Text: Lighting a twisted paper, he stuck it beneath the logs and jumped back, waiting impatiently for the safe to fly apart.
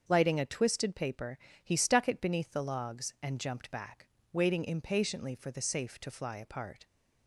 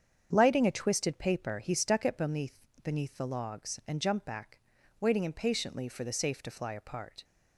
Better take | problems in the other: first | starts louder than the rest; strong; until 1.3 s; 8 dB; also in the first // says "beneath" twice; at 2.8 s

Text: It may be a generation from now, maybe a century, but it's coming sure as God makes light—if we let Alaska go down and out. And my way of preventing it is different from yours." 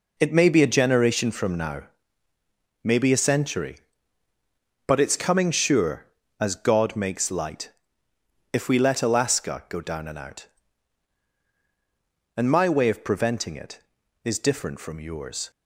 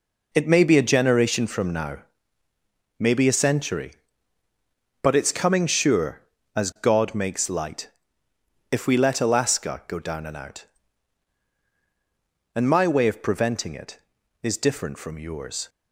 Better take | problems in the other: neither | none

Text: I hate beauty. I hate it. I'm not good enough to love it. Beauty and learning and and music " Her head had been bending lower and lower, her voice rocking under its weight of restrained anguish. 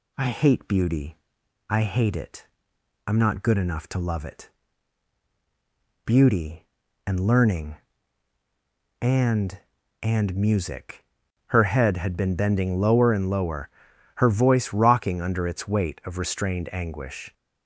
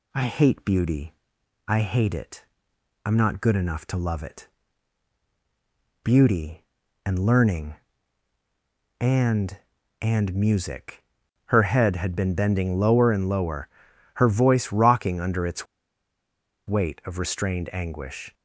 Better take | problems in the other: first | pauses between "its" and "weight"; at 15.6 s; 1.0 s long

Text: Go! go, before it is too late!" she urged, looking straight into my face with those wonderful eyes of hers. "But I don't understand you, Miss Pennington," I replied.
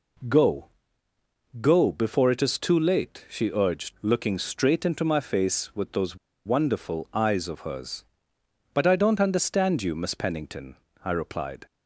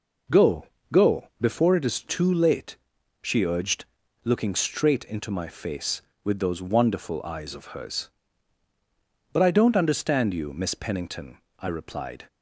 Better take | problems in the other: second | pauses between "those" and "wonderful"; slight; at 6.1 s; 0.29 s long

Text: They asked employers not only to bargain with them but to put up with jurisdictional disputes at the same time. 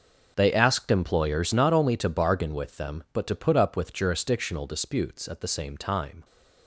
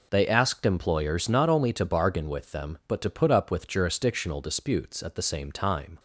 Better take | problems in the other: second | gets quieter; strong; throughout; 15 dB

